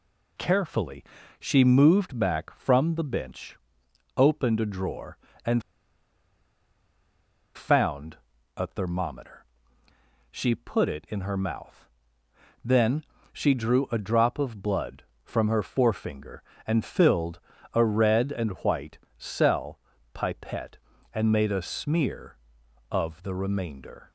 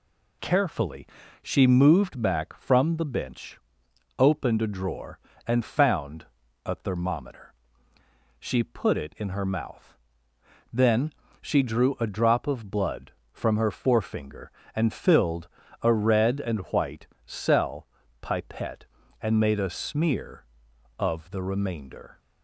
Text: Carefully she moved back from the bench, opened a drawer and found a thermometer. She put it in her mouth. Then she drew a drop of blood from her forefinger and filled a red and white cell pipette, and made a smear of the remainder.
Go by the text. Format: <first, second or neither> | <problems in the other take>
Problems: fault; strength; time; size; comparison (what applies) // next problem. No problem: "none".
second | pauses between "Carefully" and "she"; slight; at 1.0 s; 0.36 s long; slight in the second // pauses between "and" and "found"; strong; at 5.6 s; 1.9 s long // pauses between "found" and "a"; at 8.1 s; 0.40 s long; also in the second // pauses between "Then" and "she"; slight; at 13.0 s; 0.28 s long; slight in the second // pauses between "filled" and "a"; slight; at 17.3 s; 0.34 s long; slight in the second // pauses between "white" and "cell"; slight; at 18.9 s; 0.20 s long; slight in the second // pauses between "cell" and "pipette"; slight; at 19.7 s; 0.34 s long; slight in the second